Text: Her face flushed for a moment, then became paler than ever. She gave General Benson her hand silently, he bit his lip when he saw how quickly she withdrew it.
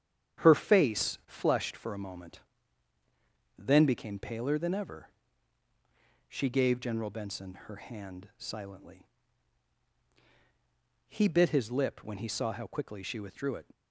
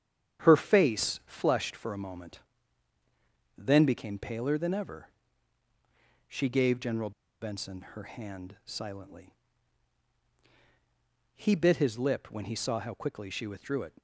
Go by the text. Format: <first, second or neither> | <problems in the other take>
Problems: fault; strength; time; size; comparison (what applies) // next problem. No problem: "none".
first | starts louder than the rest; strong; until 1.4 s; 9 dB; strong in the first // pauses between "General" and "Benson"; slight; at 7.1 s; 0.30 s long